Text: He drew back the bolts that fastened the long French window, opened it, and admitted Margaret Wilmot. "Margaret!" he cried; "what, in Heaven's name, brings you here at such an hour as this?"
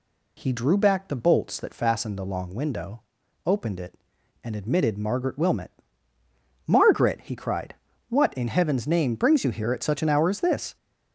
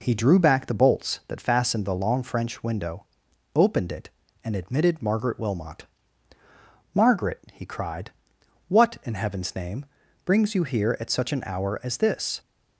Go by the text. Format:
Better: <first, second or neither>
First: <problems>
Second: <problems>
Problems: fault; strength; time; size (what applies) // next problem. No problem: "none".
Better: second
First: skips "French"; at 2.5 s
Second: none